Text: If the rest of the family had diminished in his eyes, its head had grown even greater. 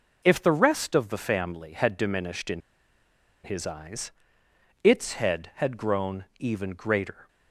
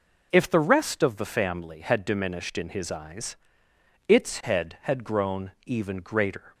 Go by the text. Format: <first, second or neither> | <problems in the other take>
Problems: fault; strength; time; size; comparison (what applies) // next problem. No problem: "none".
second | pauses between "in" and "his"; noticeable; at 2.6 s; 0.83 s long